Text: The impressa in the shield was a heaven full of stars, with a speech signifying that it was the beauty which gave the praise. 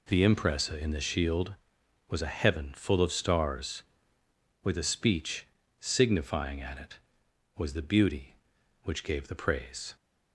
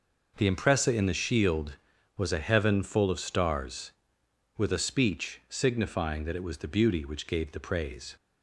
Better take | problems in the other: second | pauses between "speech" and "signifying"; slight; at 5.4 s; 0.36 s long // says "at" for "that"; at 6.6 s

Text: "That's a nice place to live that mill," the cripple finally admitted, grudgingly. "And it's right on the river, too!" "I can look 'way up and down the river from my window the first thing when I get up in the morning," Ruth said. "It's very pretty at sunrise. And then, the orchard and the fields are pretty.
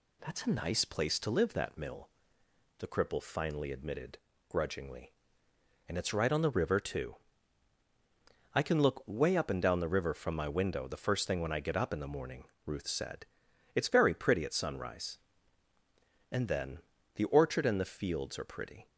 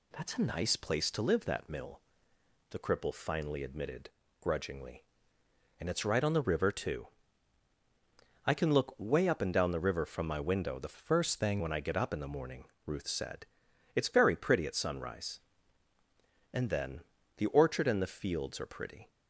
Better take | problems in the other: first | changes voice from "first" to "thing"; from 10.9 to 11.6 s; 0.7 s long

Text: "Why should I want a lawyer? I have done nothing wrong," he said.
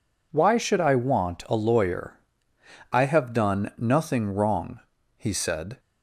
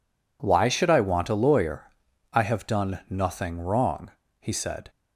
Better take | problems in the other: neither | none

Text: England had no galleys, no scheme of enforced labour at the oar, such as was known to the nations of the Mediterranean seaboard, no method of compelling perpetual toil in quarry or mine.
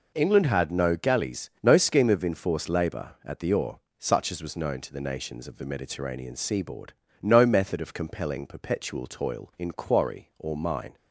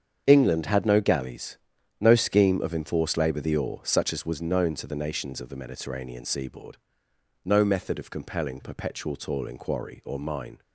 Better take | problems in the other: first | starts louder than the rest; strong; until 1.2 s; 7.5 dB // skips "at"; at 3.4 s

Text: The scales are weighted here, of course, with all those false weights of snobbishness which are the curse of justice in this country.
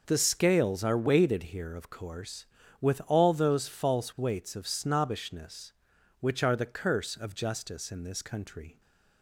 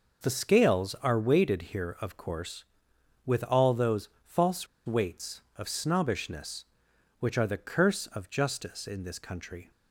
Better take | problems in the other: first | pauses between "those" and "false"; slight; at 4.0 s; 0.16 s long // pauses between "false" and "weights"; slight; at 4.6 s; 0.20 s long

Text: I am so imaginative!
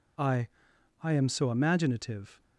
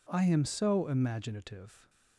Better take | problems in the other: second | says "I" twice; at 1.0 s

